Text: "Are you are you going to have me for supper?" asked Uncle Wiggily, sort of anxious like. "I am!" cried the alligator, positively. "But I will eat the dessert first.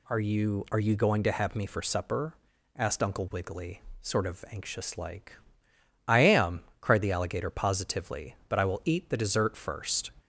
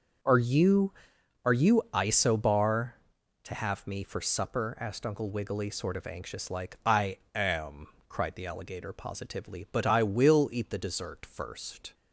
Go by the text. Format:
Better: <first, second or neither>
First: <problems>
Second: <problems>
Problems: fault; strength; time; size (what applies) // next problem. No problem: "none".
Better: first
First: none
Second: says "isobar" for "going"; at 1.9 s // pauses between "I" and "am"; slight; at 7.1 s; 0.16 s long